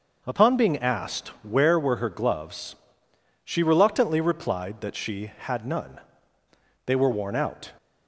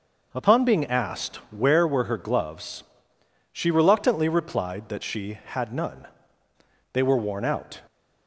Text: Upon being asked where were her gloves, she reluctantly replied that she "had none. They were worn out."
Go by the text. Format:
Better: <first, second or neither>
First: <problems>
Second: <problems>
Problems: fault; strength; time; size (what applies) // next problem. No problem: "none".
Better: neither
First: none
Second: none